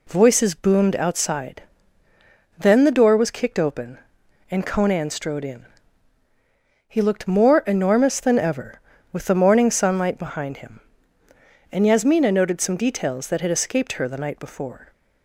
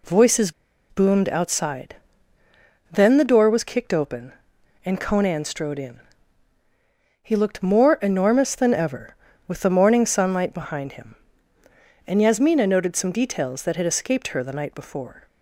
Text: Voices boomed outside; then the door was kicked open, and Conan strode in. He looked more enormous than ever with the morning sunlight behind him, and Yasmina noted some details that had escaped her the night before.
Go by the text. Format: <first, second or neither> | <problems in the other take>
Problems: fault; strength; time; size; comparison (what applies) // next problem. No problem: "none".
first | pauses between "Voices" and "boomed"; at 0.5 s; 0.39 s long